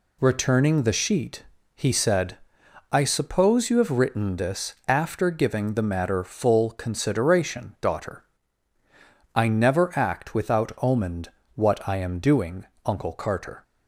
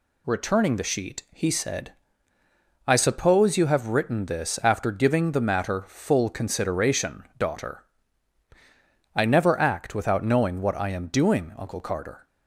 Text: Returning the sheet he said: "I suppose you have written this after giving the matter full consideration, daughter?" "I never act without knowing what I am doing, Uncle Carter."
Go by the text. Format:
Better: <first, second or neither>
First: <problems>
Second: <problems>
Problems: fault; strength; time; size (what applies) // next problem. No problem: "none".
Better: second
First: pauses between "sheet" and "he"; slight; at 1.4 s; 0.32 s long // says "omened" for "knowing"; at 10.8 s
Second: none